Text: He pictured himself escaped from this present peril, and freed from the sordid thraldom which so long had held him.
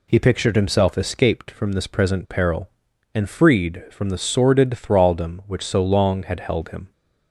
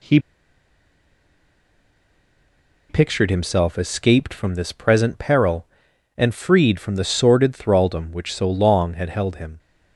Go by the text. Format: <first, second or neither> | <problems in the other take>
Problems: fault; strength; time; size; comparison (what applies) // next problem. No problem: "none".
first | pauses between "He" and "pictured"; strong; at 0.1 s; 2.7 s long